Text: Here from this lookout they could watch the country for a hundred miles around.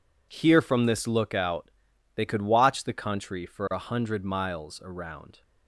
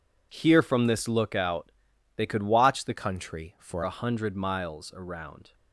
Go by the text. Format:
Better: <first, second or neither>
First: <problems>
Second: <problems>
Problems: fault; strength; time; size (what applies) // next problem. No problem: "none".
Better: first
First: pauses between "lookout" and "they"; at 1.7 s; 0.44 s long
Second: pauses between "lookout" and "they"; at 1.7 s; 0.44 s long // changes voice from "country" to "for"; from 2.9 to 3.8 s; 0.9 s long